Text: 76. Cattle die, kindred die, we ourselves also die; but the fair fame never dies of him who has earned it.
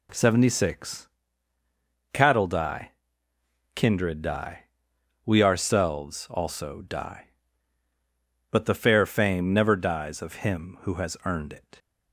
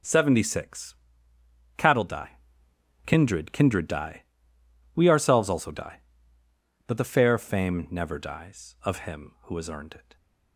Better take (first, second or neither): first